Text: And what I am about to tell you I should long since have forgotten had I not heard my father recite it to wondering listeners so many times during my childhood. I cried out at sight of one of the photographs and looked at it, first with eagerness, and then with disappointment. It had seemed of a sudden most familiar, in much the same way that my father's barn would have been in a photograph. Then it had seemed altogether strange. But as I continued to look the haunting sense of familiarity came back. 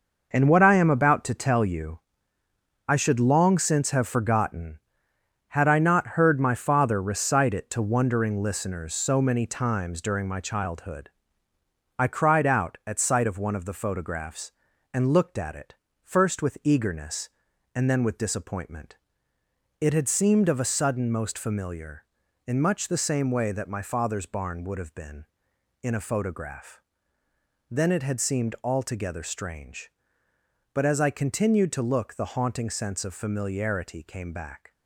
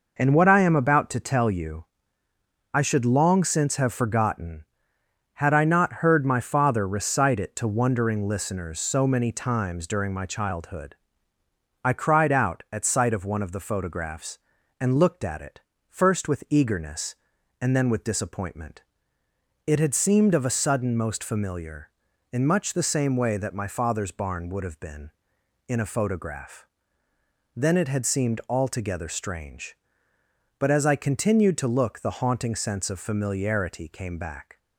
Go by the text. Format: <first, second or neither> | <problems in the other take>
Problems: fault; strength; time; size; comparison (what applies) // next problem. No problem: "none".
second | gets quieter; strong; throughout; 9 dB // pauses between "you" and "I"; noticeable; at 1.9 s; 0.88 s long; noticeable in the second